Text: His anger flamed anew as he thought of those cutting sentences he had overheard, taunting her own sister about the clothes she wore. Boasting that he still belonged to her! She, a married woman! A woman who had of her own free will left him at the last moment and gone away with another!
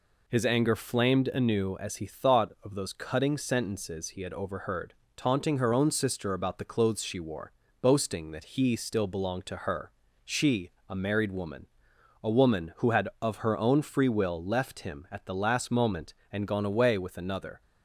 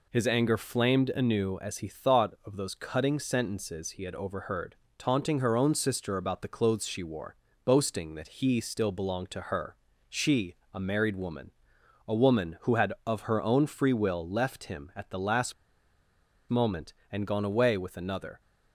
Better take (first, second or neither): first